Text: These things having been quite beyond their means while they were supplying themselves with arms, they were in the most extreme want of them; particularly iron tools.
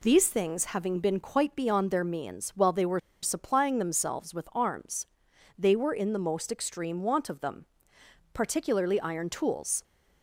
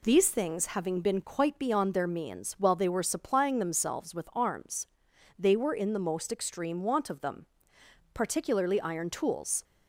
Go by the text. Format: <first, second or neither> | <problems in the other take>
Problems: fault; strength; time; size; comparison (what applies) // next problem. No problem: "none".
second | pauses between "were" and "supplying"; slight; at 2.9 s; 0.24 s long